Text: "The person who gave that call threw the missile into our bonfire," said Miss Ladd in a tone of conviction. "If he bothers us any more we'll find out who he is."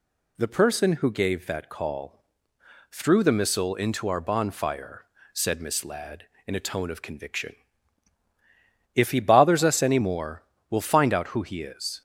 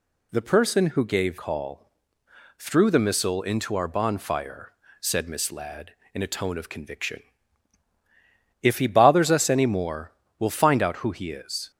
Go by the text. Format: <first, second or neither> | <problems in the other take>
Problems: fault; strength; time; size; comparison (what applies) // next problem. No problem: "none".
first | skips "that"; at 1.3 s // pauses between "call" and "threw"; noticeable; at 1.9 s; 0.68 s long; noticeable in the first // pauses between "more" and "we'll"; slight; at 10.1 s; 0.26 s long; slight in the first